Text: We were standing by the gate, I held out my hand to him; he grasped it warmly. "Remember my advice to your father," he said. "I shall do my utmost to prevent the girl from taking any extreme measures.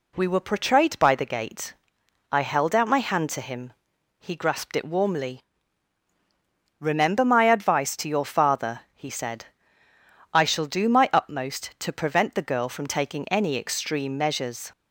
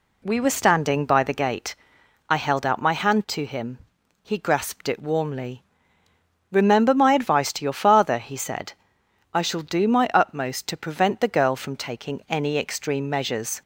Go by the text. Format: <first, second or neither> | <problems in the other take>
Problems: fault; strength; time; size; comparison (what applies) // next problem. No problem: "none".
second | says "portrayed" for "standing"; at 0.4 s